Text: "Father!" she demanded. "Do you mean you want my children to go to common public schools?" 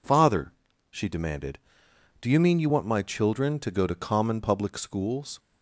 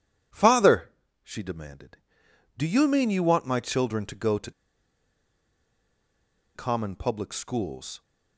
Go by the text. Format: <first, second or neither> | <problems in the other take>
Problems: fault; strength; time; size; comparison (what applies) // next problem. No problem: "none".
first | pauses between "to" and "common"; strong; at 4.5 s; 2.0 s long